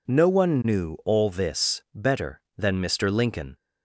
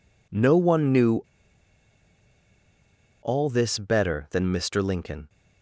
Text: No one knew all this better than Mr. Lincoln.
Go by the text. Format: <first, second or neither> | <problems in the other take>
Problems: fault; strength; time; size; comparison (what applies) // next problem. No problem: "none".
first | pauses between "knew" and "all"; strong; at 1.2 s; 2.0 s long